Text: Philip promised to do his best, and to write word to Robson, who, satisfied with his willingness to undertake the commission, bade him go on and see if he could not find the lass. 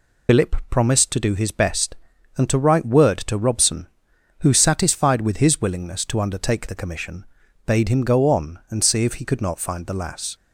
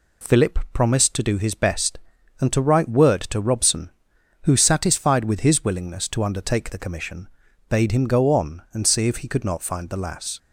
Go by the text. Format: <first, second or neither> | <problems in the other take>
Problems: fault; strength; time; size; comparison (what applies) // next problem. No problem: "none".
second | loses the start of "Philip"; at 0.2 s; 110 ms